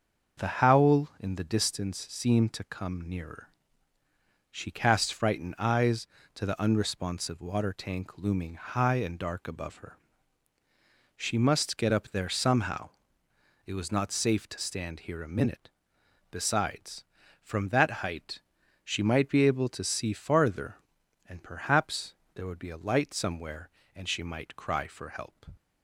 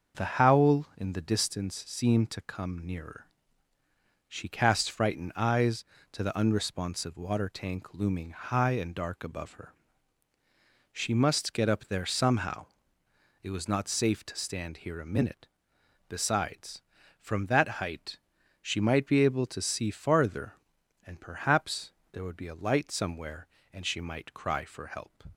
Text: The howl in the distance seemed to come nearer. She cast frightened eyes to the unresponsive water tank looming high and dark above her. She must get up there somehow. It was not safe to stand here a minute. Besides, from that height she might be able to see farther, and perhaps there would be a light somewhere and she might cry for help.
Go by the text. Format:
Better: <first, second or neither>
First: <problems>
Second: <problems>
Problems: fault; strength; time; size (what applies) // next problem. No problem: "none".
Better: neither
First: starts louder than the rest; until 1.5 s; 6 dB // pauses between "height" and "she"; at 18.4 s; 0.44 s long // pauses between "perhaps" and "there"; slight; at 22.1 s; 0.22 s long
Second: starts louder than the rest; until 1.3 s; 6.5 dB // pauses between "height" and "she"; at 18.1 s; 0.44 s long // pauses between "perhaps" and "there"; slight; at 21.9 s; 0.22 s long